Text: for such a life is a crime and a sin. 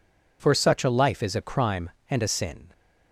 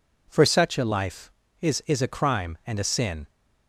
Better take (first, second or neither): first